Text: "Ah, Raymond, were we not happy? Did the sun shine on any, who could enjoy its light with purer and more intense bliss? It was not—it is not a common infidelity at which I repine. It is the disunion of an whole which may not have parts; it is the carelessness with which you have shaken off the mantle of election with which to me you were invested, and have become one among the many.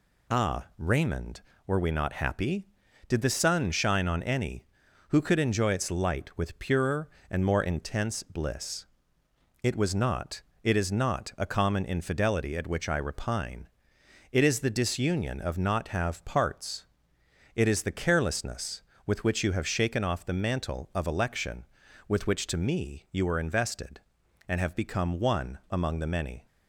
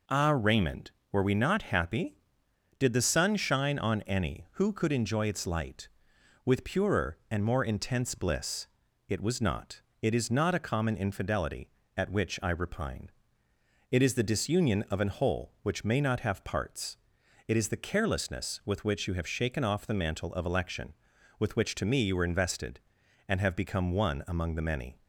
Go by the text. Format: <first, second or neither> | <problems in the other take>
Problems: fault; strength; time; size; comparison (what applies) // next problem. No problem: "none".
second | skips "an whole which may"; at 15.5 s